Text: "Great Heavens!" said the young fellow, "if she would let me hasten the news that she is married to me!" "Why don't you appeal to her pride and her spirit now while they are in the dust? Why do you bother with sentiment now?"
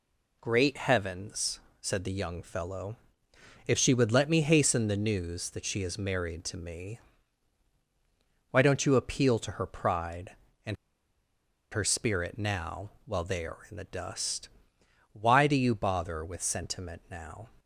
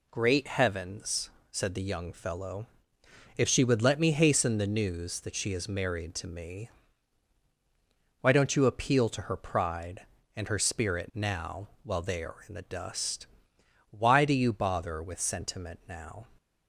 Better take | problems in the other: second | pauses between "and" and "her"; noticeable; at 10.7 s; 0.98 s long

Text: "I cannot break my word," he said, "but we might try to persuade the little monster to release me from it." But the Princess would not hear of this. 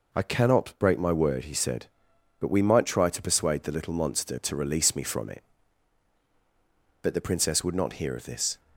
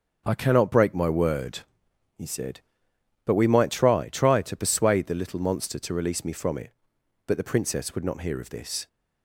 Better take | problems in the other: first | starts louder than the rest; until 1.2 s; 6.5 dB // says "try" twice; at 4.0 s

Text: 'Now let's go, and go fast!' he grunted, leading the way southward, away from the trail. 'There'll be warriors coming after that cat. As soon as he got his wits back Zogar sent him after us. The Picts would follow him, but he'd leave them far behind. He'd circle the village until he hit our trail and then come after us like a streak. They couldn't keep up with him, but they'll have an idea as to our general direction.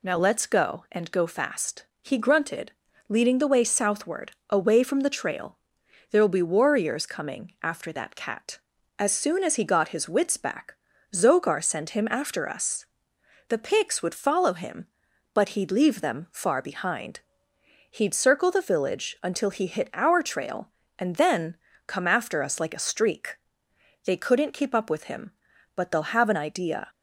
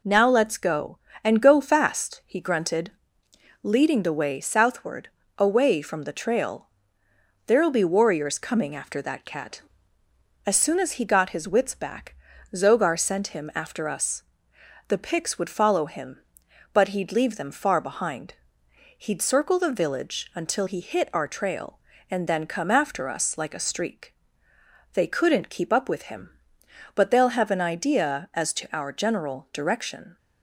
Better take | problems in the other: second | pauses between "back" and "Zogar"; at 10.7 s; 0.38 s long; also in the second // pauses between "then" and "come"; slight; at 21.5 s; 0.32 s long // stops before "as to our general direction"; at 26.8 s

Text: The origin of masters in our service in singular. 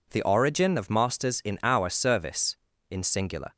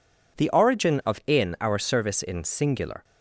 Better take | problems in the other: first | skips "masters"; at 1.2 s

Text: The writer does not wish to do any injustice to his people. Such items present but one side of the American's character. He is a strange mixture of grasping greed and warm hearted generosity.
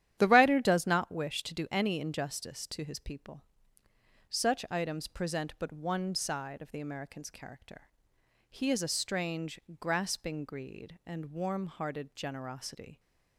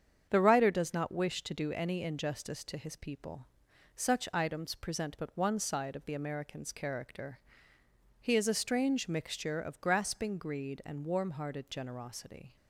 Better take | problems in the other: second | starts louder than the rest; strong; until 1.2 s; 11 dB; strong in the second // skips "mixture of"; at 9.6 s

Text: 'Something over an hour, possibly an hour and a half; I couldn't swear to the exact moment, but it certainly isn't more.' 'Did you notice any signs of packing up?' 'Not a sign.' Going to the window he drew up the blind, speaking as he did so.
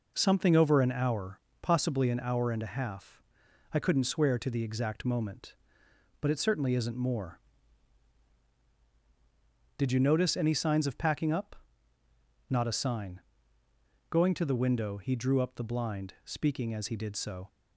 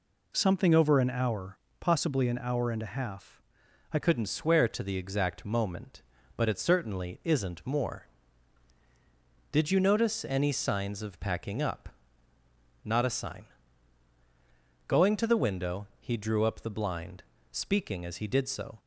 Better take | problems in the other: first | changes voice at "couldn't"; from 4.0 s on; 14.7 s long

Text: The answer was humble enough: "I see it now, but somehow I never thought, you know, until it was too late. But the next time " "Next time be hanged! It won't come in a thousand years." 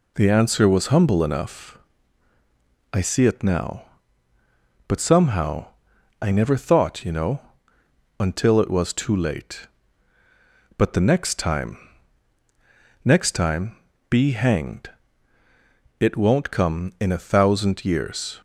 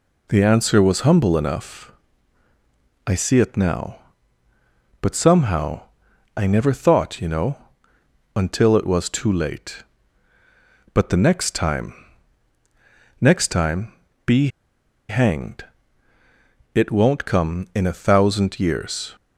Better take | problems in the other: first | pauses between "somehow" and "I"; noticeable; at 5.8 s; 0.54 s long; noticeable in the first // pauses between "time" and "be"; slight; at 13.9 s; 0.32 s long; slight in the first // pauses between "be" and "hanged"; noticeable; at 14.4 s; 0.61 s long

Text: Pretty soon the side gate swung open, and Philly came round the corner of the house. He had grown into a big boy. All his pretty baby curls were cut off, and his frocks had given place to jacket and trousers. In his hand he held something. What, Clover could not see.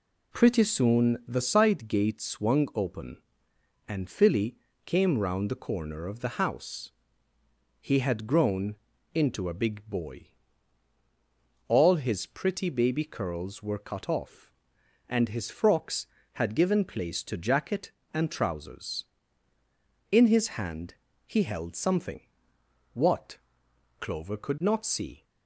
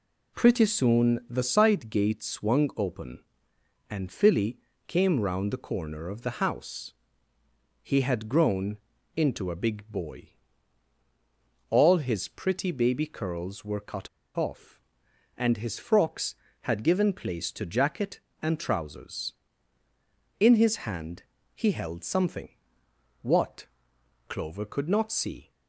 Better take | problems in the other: first | pauses between "Philly" and "came"; slight; at 4.5 s; 0.30 s long; slight in the first // pauses between "grown" and "into"; at 8.7 s; 0.38 s long; also in the first // pauses between "cut" and "off"; slight; at 14.0 s; 0.29 s long // pauses between "hand" and "he"; slight; at 21.2 s; 0.30 s long; slight in the first

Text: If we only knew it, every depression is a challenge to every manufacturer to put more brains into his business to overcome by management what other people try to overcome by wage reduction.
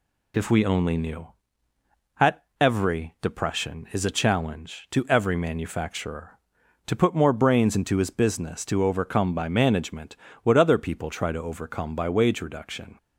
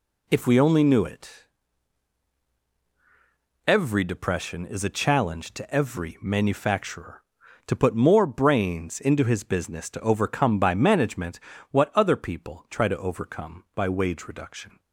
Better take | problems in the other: second | says "at" for "it"; at 2.1 s // pauses between "management" and "what"; slight; at 10.1 s; 0.26 s long; slight in the second

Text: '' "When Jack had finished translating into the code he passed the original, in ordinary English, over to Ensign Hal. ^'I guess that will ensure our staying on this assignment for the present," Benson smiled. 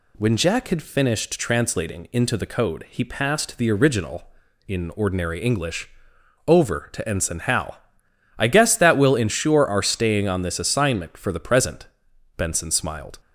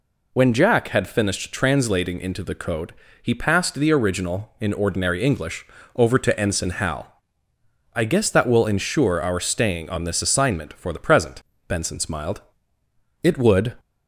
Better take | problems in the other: first | pauses between "code" and "he"; slight; at 2.9 s; 0.26 s long // goes on to say "It would"; from 13.2 s on; 0.54 s long

